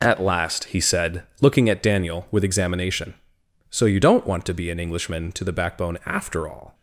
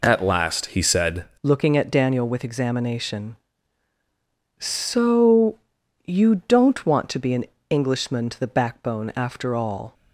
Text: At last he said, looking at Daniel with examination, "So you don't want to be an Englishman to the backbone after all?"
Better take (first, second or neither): first